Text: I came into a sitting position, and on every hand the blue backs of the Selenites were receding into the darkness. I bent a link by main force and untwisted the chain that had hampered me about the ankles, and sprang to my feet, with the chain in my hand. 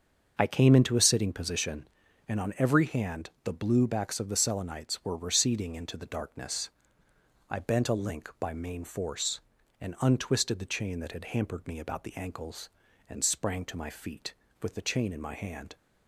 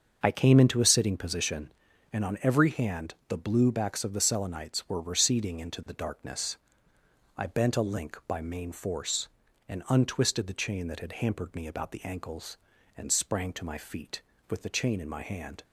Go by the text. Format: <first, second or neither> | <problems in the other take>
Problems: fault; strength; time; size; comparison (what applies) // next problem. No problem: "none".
neither | starts louder than the rest; the same in both